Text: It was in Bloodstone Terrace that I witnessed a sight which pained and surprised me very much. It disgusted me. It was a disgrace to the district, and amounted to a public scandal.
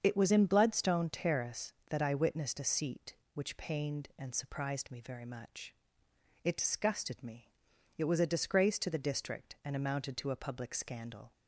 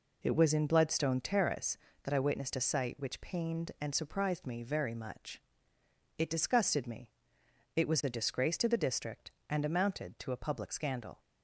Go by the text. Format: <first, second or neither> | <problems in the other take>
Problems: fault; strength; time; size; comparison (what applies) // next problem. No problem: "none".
second | starts louder than the rest; until 1.0 s; 7 dB // says "seat" for "sight"; at 2.6 s